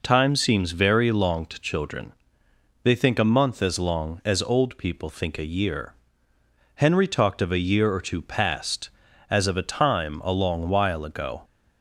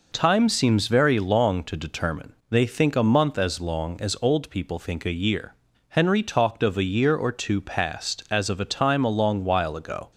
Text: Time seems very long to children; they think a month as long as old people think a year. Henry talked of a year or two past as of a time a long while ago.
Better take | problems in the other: first | says "determine" for "children"; at 1.7 s

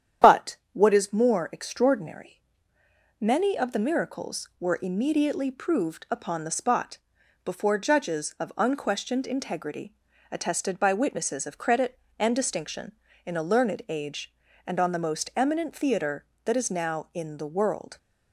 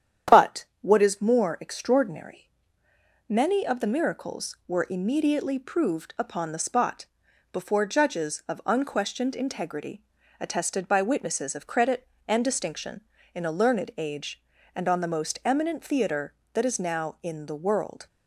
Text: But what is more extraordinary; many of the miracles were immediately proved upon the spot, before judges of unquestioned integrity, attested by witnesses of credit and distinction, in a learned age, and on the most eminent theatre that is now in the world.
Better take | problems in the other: second | loses the start of "But"; at 0.2 s; 20 ms // starts louder than the rest; strong; until 1.4 s; 9.5 dB; strong in the second // pauses between "But" and "what"; slight; at 0.5 s; 0.18 s long; slight in the second

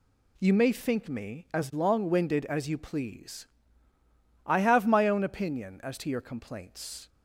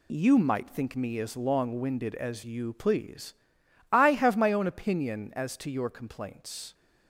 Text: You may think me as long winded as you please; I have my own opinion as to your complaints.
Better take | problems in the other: first | says "might" for "may"; at 0.3 s

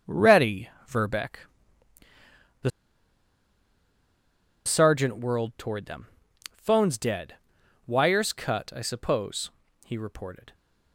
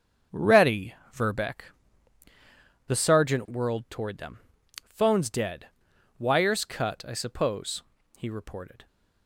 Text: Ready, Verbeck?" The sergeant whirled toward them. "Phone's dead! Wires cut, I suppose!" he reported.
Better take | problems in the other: second | starts louder than the rest; strong; until 1.2 s; 7 dB; strong in the second // pauses between "The" and "sergeant"; strong; at 2.6 s; 1.9 s long

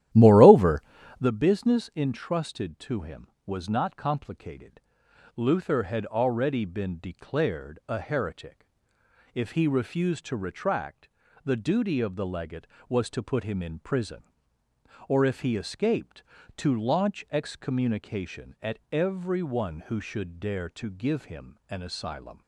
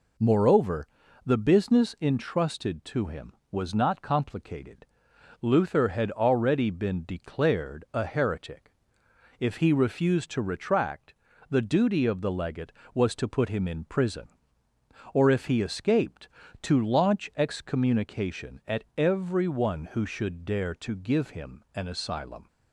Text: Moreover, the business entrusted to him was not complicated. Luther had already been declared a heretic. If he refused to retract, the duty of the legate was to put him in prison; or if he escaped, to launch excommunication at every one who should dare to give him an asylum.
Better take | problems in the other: second | starts louder than the rest; strong; until 1.3 s; 12.5 dB

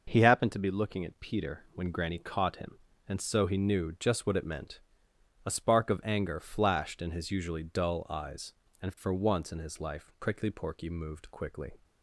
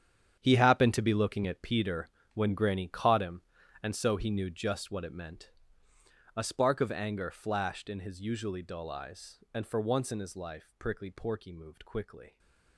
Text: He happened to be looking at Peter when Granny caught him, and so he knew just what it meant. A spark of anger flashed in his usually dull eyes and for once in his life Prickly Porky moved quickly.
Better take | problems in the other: first | gets quieter; strong; throughout; 13.5 dB // pauses between "Peter" and "when"; slight; at 2.0 s; 0.26 s long

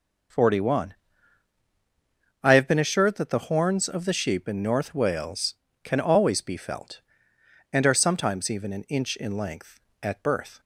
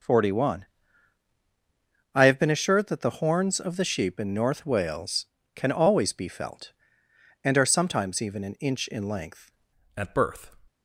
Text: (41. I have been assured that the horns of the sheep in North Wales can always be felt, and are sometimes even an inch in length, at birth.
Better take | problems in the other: first | changes voice at "at"; from 9.9 s on; 0.6 s long

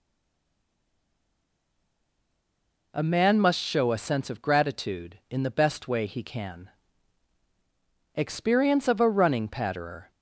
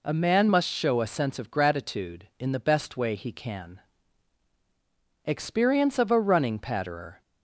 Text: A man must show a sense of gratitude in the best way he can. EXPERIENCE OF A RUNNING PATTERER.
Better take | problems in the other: second | stays silent before the first word; strong; until 2.9 s; 2.9 s long

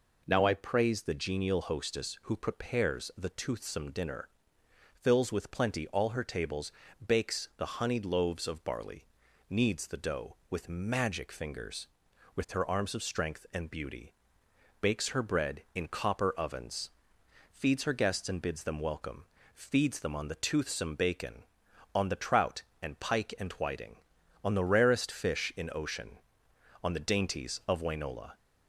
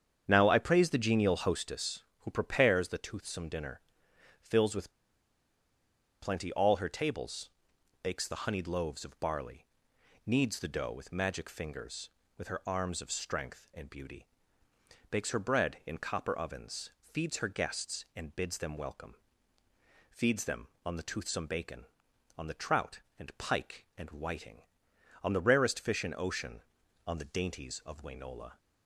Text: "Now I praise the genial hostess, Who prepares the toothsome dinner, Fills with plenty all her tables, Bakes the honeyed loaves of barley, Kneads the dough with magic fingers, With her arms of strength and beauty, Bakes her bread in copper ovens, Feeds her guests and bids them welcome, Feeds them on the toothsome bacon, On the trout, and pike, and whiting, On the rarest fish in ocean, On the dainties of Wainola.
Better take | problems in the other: first | starts louder than the rest; strong; until 1.2 s; 8 dB // pauses between "with" and "plenty"; strong; at 4.9 s; 1.3 s long

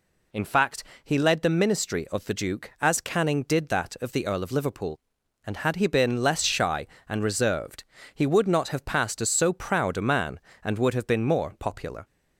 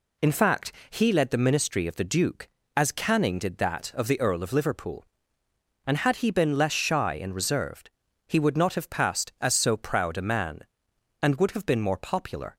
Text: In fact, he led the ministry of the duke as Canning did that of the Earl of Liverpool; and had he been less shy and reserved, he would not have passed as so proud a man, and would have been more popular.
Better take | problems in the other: neither | none

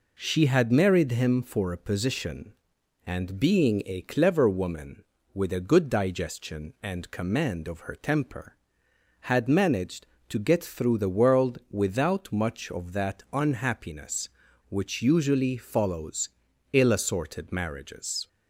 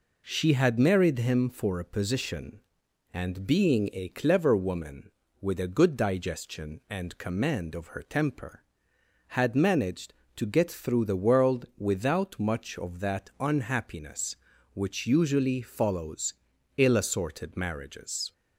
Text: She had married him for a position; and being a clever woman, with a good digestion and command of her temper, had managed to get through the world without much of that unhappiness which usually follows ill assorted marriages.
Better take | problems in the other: neither | pauses between "follows" and "ill"; noticeable; the same in both

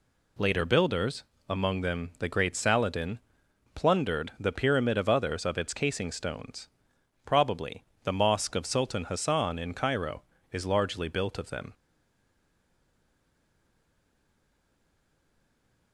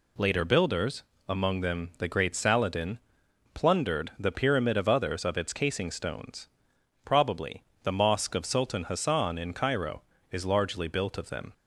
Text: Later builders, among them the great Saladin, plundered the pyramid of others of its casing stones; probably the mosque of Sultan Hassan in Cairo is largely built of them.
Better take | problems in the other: second | pauses between "probably" and "the"; slight; at 7.8 s; 0.18 s long; slight in the second // stays silent after the last word; strong; from 11.7 s on; 4.2 s long

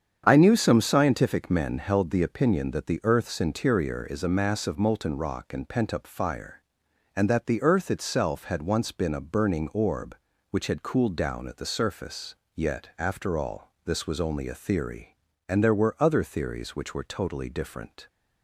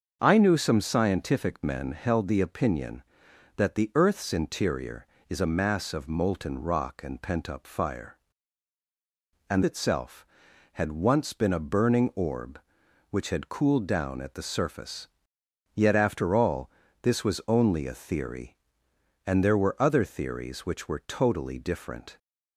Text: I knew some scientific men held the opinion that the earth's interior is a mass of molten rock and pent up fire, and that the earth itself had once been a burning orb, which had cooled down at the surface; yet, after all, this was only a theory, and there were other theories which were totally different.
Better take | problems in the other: first | starts louder than the rest; until 1.2 s; 6.5 dB; strong in the first // skips "that the earth"; at 9.6 s

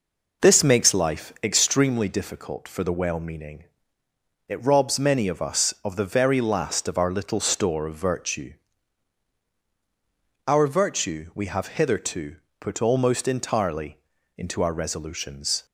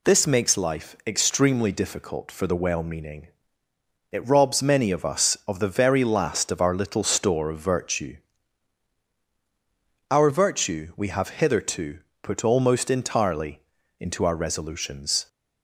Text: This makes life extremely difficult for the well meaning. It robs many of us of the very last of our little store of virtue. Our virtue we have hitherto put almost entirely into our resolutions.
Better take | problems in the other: second | starts louder than the rest; noticeable; until 1.8 s; 5 dB // pauses between "hitherto" and "put"; slight; at 12.3 s; 0.24 s long; slight in the second // pauses between "entirely" and "into"; at 13.9 s; 0.40 s long; also in the second

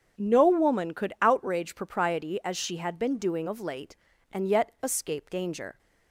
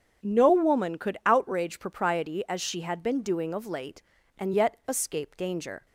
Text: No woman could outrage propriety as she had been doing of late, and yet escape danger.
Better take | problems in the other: neither | starts louder than the rest; strong; the same in both

